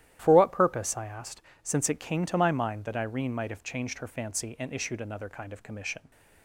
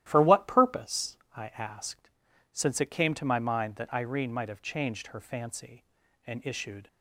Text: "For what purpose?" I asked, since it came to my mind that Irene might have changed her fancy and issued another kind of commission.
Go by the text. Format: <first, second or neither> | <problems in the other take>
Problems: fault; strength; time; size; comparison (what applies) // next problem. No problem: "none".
first | starts louder than the rest; strong; until 1.0 s; 13.5 dB; strong in the first // stops before "another kind of commission"; at 6.8 s